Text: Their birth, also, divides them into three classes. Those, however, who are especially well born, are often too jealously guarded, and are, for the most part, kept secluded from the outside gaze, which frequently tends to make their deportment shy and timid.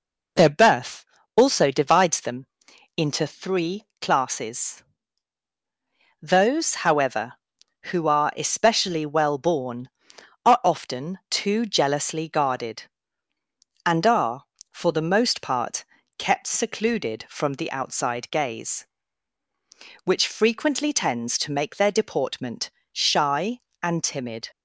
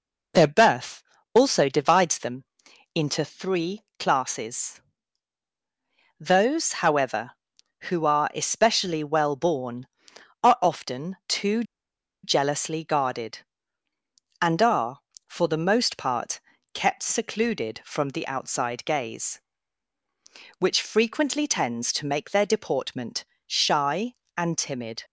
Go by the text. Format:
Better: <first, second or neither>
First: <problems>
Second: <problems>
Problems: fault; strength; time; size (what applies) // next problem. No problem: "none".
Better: first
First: pauses between "them" and "into"; noticeable; at 2.4 s; 0.50 s long // pauses between "three" and "classes"; slight; at 3.8 s; 0.16 s long // pauses between "deportment" and "shy"; slight; at 22.7 s; 0.22 s long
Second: pauses between "them" and "into"; noticeable; at 2.4 s; 0.50 s long // pauses between "three" and "classes"; slight; at 3.8 s; 0.16 s long // pauses between "too" and "jealously"; noticeable; at 11.6 s; 0.60 s long // pauses between "deportment" and "shy"; slight; at 23.2 s; 0.22 s long